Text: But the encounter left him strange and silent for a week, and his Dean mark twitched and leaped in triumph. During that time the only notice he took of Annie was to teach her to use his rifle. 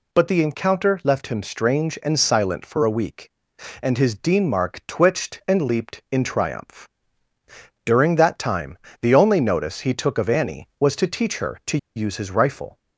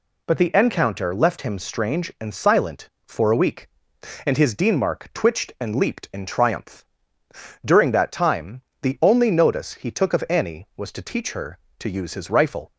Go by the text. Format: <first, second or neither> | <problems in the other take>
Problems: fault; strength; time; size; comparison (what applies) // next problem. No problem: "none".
second | pauses between "time" and "the"; slight; at 8.7 s; 0.24 s long; slight in the second // pauses between "to" and "use"; slight; at 11.7 s; 0.18 s long